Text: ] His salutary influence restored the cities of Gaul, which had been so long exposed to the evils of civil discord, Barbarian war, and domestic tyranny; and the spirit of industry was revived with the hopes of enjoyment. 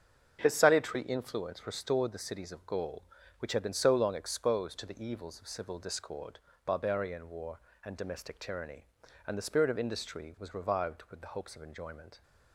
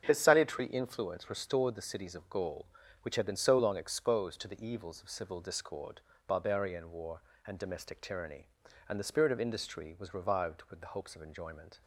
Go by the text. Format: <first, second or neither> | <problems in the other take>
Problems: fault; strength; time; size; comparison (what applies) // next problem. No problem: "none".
neither | starts louder than the rest; the same in both